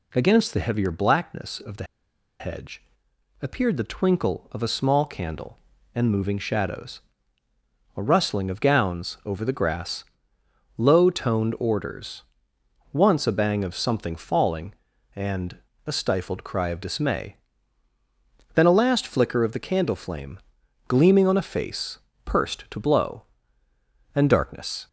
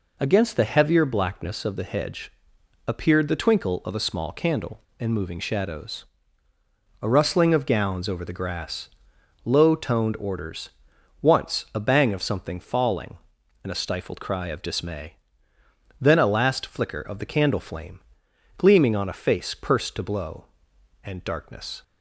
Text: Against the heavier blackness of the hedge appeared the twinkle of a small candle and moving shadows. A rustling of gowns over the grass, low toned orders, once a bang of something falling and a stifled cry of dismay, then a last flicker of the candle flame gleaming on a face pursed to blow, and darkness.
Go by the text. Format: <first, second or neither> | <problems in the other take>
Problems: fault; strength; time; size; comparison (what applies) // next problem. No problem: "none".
second | pauses between "the" and "hedge"; noticeable; at 1.8 s; 0.56 s long // pauses between "hedge" and "appeared"; noticeable; at 2.8 s; 0.60 s long; noticeable in the second // pauses between "and" and "a"; slight; at 15.5 s; 0.26 s long // pauses between "flame" and "gleaming"; noticeable; at 20.3 s; 0.48 s long; noticeable in the second // pauses between "face" and "pursed"; slight; at 21.9 s; 0.24 s long